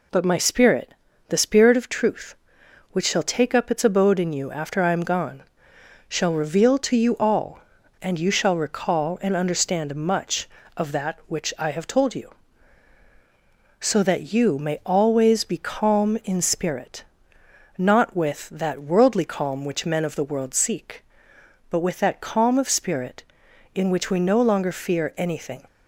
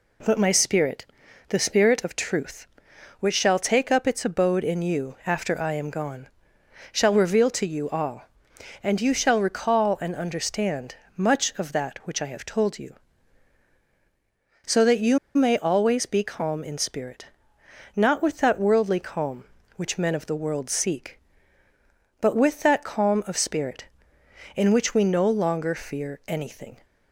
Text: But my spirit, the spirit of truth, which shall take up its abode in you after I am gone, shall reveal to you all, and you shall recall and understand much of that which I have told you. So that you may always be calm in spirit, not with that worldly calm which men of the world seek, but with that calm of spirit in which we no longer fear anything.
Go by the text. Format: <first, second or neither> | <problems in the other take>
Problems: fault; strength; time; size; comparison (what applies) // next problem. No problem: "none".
first | pauses between "understand" and "much"; slight; at 10.9 s; 0.24 s long // pauses between "you" and "may"; slight; at 15.1 s; 0.17 s long